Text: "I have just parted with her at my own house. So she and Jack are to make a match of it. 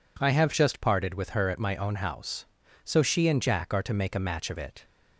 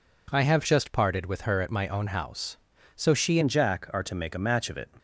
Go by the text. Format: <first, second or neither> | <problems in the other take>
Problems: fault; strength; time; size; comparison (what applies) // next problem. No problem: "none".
first | changes voice at "and"; from 3.4 s on; 1.4 s long